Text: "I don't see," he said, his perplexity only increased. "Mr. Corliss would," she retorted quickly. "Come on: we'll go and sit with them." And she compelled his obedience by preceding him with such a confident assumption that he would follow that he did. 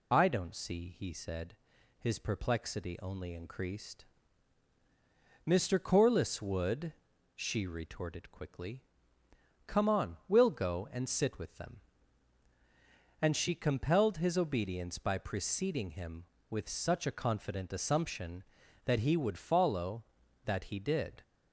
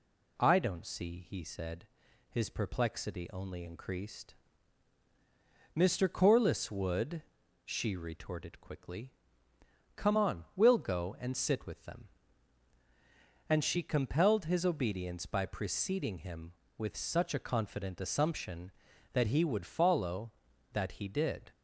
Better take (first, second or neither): second